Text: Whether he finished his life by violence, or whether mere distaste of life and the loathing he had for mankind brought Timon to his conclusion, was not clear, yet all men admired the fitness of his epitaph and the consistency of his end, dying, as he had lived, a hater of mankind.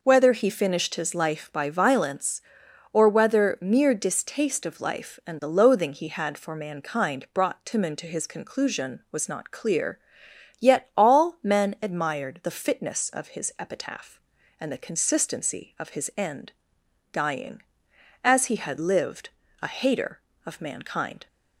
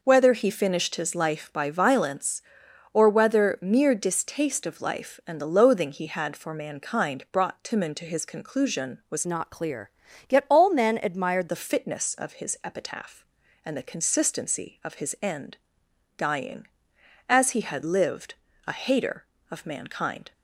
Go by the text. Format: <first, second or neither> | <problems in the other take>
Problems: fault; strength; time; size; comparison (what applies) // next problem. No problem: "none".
first | changes voice from "not" to "admired"; from 9.2 to 11.4 s; 2.2 s long